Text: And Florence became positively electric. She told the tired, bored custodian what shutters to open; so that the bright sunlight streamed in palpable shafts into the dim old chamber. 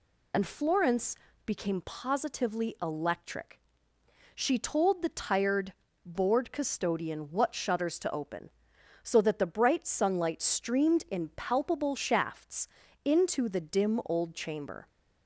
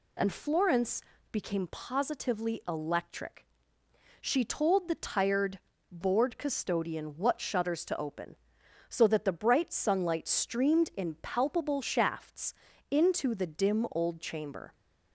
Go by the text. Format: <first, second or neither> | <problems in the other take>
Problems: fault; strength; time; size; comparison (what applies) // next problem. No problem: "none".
second | loses the start of "And"; at 0.3 s; 35 ms // pauses between "Florence" and "became"; slight; at 1.1 s; 0.30 s long; slight in the second // pauses between "shafts" and "into"; at 12.6 s; 0.38 s long; also in the second